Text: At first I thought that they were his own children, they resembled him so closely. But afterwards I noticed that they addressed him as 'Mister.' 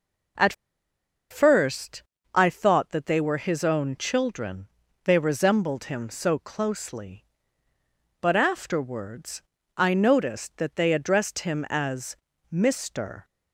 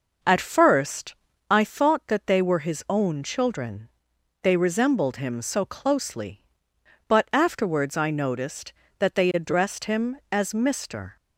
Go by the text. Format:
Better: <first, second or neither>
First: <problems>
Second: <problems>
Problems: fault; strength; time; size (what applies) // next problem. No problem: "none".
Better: second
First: pauses between "At" and "first"; noticeable; at 0.5 s; 0.77 s long // pauses between "first" and "I"; slight; at 2.0 s; 0.32 s long // pauses between "afterwards" and "I"; slight; at 9.4 s; 0.34 s long // pauses between "as" and "Mister"; slight; at 12.1 s; 0.36 s long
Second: pauses between "first" and "I"; slight; at 1.1 s; 0.34 s long